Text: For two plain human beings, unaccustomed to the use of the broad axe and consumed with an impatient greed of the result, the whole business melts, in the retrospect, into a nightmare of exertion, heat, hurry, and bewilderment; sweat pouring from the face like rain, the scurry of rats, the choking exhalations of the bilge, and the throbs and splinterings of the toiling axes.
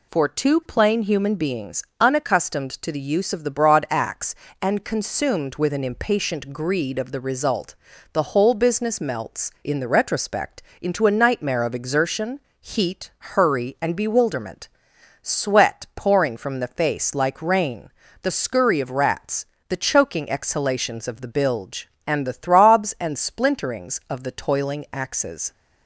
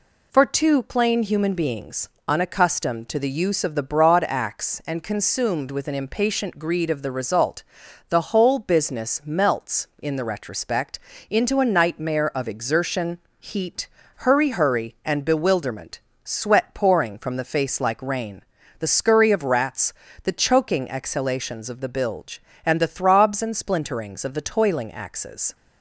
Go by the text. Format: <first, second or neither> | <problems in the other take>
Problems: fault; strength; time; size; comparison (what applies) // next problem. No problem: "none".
first | says "hurry" twice; at 14.4 s